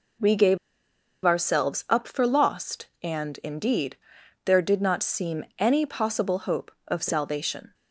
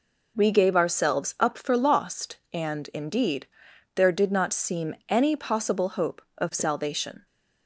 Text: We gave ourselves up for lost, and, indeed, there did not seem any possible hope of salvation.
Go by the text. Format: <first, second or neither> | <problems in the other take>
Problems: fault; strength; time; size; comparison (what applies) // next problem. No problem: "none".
second | pauses between "gave" and "ourselves"; noticeable; at 0.5 s; 0.67 s long